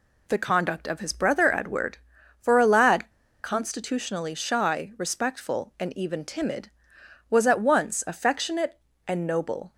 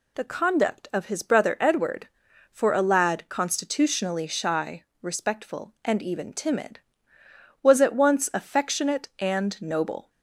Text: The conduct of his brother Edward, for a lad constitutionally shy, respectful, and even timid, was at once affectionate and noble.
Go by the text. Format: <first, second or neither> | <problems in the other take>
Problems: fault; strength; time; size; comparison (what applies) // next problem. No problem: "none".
second | pauses between "lad" and "constitutionally"; slight; at 3.1 s; 0.31 s long